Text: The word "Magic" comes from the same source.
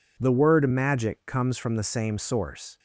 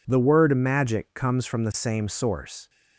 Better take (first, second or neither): neither